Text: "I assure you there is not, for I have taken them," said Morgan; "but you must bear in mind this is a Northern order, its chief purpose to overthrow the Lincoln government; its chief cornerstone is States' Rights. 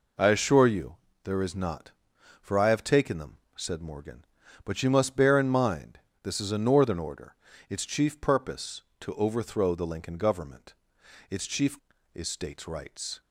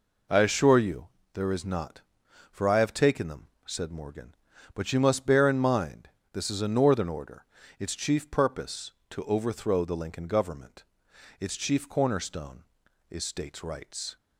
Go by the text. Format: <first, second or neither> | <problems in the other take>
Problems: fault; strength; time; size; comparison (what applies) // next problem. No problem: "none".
second | pauses between "you" and "there"; slight; at 0.9 s; 0.28 s long; slight in the second // pauses between "mind" and "this"; slight; at 5.9 s; 0.24 s long; slight in the second // skips "cornerstone"; at 11.9 s